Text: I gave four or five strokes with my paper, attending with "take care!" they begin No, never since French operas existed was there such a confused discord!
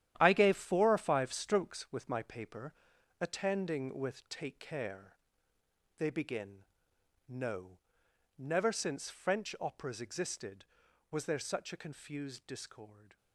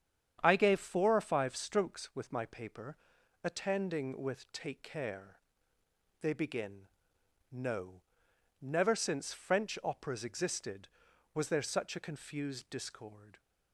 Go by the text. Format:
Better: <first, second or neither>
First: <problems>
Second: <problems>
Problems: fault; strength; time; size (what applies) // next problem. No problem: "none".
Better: second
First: gets quieter; strong; throughout; 10.5 dB // starts louder than the rest; strong; until 1.1 s; 11.5 dB // pauses between "begin" and "No"; noticeable; at 6.6 s; 0.64 s long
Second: starts louder than the rest; strong; until 1.4 s; 8.5 dB // pauses between "begin" and "No"; noticeable; at 6.8 s; 0.64 s long